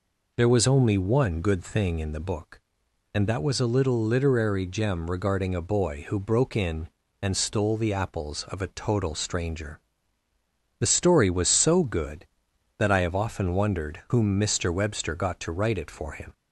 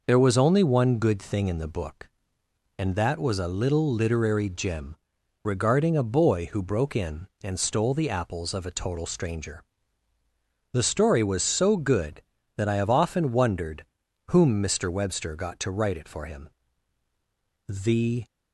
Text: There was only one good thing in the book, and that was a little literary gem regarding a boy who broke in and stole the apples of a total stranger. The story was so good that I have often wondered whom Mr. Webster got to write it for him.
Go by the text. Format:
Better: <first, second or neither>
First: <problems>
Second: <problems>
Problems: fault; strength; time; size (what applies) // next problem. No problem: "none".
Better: first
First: none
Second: pauses between "gem" and "regarding"; noticeable; at 4.9 s; 0.48 s long // pauses between "wondered" and "whom"; at 13.8 s; 0.42 s long // goes on to say "The"; from 17.6 s on; 0.58 s long